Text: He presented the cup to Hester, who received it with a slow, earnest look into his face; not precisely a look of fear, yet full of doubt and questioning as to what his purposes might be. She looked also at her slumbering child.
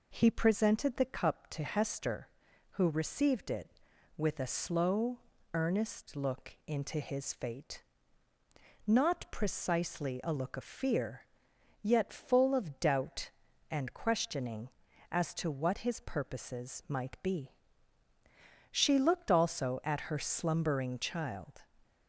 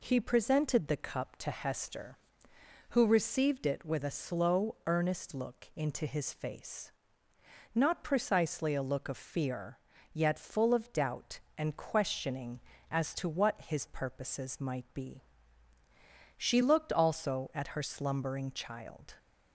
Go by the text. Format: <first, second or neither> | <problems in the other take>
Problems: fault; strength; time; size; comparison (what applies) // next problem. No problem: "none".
second | says "fate" for "face"; at 7.3 s